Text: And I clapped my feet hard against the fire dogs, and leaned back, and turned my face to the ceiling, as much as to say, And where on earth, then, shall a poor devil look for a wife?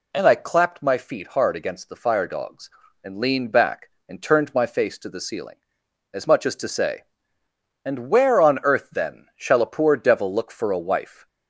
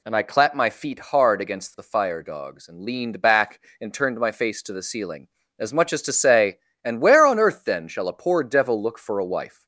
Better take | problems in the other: neither | none

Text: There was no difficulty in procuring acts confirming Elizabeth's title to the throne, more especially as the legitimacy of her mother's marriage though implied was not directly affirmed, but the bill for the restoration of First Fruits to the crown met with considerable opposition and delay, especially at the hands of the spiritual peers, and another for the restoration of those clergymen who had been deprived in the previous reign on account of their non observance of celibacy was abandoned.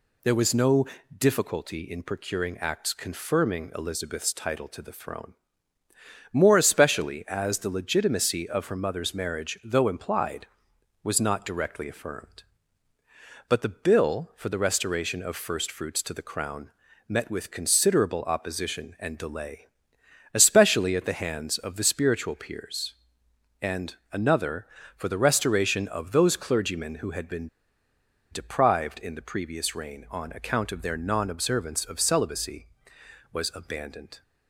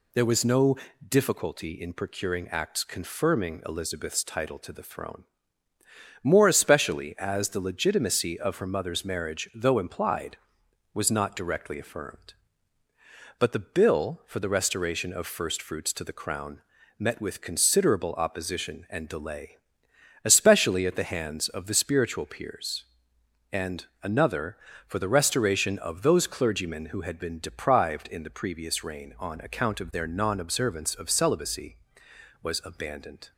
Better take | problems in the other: second | pauses between "no" and "difficulty"; slight; at 0.8 s; 0.30 s long; slight in the second // pauses between "crown" and "met"; at 16.6 s; 0.38 s long; also in the second // pauses between "and" and "another"; slight; at 23.9 s; 0.16 s long; slight in the second // pauses between "been" and "deprived"; noticeable; at 27.4 s; 0.83 s long

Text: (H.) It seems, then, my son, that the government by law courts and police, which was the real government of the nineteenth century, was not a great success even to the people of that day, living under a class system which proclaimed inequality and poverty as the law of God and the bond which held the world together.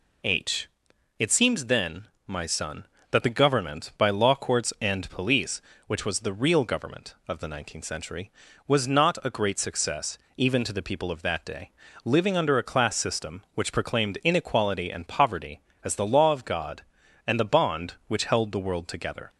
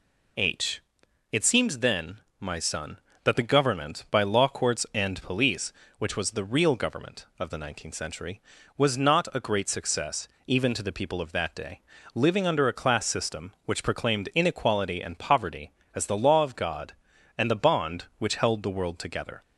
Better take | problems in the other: neither | pauses between "success" and "even"; slight; the same in both

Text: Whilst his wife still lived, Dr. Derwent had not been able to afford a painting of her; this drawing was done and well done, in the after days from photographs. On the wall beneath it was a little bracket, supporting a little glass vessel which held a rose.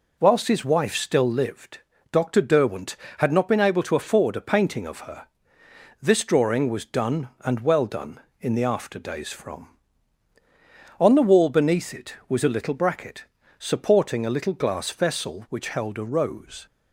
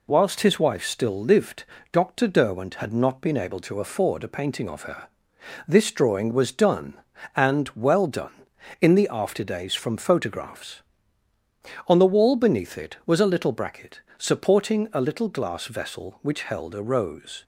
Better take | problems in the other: second | skips "photographs"; at 10.3 s

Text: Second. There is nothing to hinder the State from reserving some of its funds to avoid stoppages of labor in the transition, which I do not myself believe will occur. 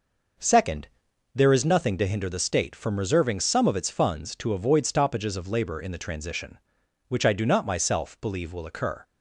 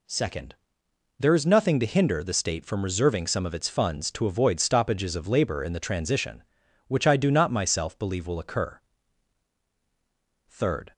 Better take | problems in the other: first | goes on to say "Third"; slight; from 10.4 s on; 0.44 s long

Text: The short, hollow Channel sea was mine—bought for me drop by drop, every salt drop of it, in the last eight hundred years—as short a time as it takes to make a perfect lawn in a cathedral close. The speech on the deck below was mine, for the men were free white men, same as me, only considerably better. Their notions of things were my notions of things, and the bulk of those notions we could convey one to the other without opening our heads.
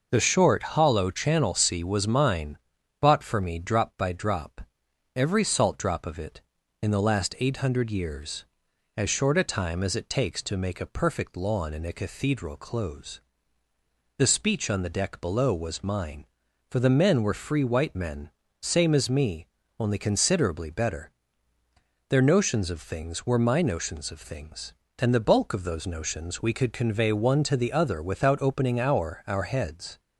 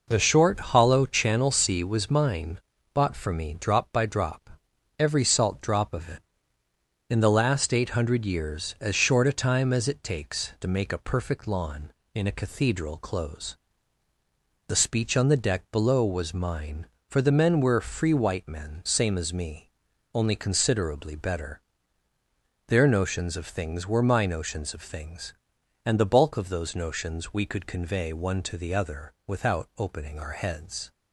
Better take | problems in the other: second | says "our" twice; at 29.2 s

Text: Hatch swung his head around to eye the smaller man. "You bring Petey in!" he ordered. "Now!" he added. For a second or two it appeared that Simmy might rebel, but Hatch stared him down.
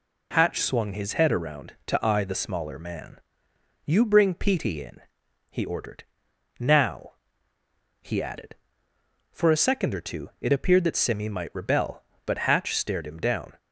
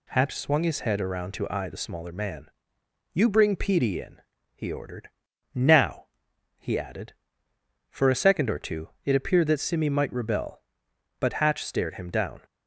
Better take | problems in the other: neither | none

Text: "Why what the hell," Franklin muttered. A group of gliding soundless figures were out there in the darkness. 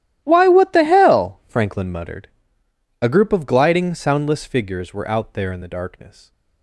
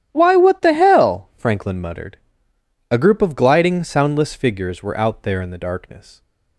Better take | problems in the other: second | gets quieter; strong; throughout; 18.5 dB // starts louder than the rest; strong; until 1.2 s; 12.5 dB; strong in the second

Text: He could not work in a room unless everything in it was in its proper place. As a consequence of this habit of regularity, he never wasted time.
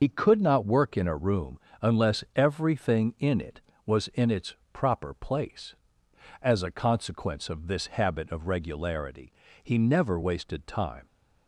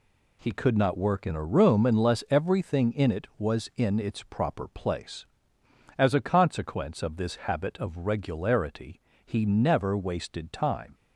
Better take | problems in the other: second | loses the start of "He"; at 0.0 s; 65 ms // starts louder than the rest; noticeable; until 1.0 s; 6 dB // pauses between "room" and "unless"; slight; at 1.5 s; 0.22 s long // pauses between "its" and "proper"; slight; at 4.5 s; 0.20 s long

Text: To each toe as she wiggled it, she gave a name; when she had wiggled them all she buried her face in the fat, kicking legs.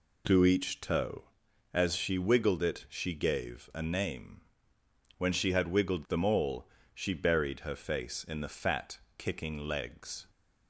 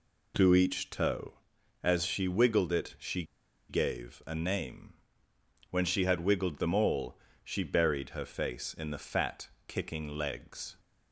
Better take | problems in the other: first | pauses between "she" and "gave"; at 3.2 s; 0.45 s long // pauses between "all" and "she"; slight; at 7.1 s; 0.24 s long; slight in the first

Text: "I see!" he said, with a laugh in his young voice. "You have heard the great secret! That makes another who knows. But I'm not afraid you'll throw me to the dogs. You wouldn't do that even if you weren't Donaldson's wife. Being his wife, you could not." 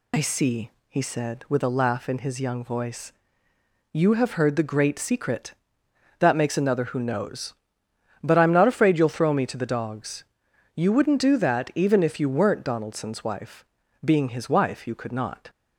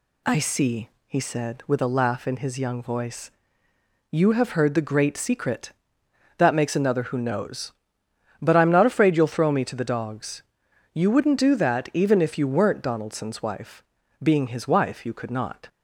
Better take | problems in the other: second | loses the start of "I"; at 0.1 s; 70 ms

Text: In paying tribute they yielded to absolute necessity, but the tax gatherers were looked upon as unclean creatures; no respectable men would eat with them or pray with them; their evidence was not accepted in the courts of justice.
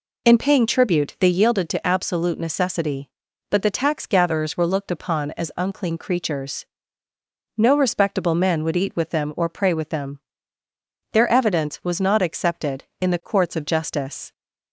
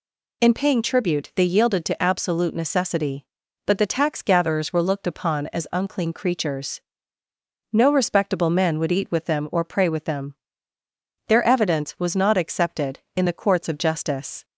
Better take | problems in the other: second | starts louder than the rest; slight; until 1.5 s; 3 dB

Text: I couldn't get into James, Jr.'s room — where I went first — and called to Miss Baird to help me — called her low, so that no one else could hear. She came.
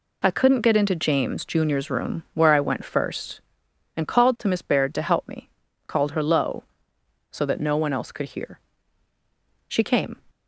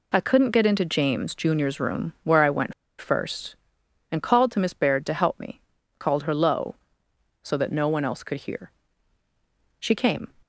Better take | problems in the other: first | pauses between "went" and "first"; slight; at 2.7 s; 0.26 s long

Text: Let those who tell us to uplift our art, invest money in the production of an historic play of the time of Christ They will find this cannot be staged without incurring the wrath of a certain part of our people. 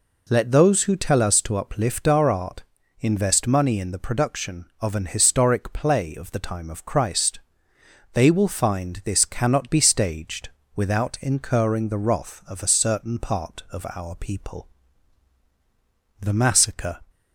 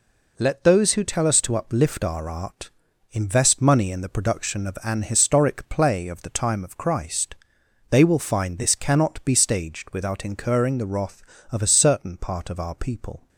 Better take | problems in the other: second | pauses between "Christ" and "They"; noticeable; at 7.3 s; 0.74 s long; noticeable in the second // pauses between "staged" and "without"; slight; at 10.4 s; 0.26 s long // goes on to say "The Massacre"; noticeable; from 16.2 s on; 0.78 s long

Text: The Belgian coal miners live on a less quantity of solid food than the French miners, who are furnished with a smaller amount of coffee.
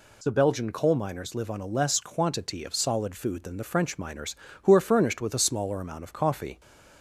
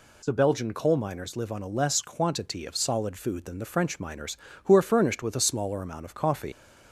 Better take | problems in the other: first | leaves "coffee" unfinished; at 6.5 s; 90 ms

